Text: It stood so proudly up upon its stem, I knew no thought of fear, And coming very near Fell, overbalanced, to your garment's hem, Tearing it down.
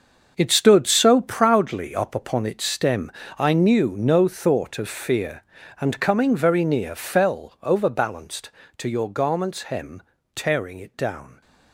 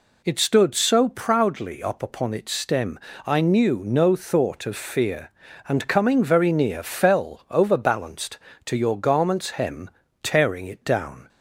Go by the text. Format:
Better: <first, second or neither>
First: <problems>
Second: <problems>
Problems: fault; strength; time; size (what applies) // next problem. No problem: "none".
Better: second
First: gets quieter; strong; throughout; 11.5 dB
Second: none